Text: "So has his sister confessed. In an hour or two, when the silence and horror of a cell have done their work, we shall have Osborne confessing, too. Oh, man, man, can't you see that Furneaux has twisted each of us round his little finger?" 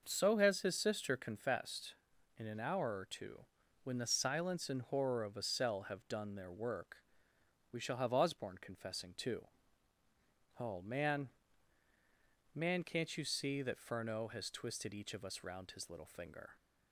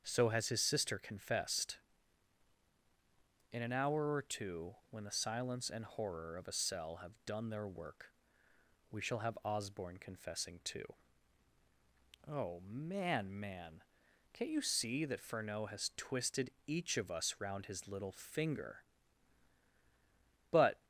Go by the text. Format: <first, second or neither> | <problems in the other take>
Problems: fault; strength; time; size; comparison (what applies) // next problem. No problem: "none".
first | starts louder than the rest; until 1.0 s; 7 dB // pauses between "twisted" and "each"; slight; at 16.5 s; 0.16 s long // goes on to say "But"; slight; from 20.5 s on; 0.34 s long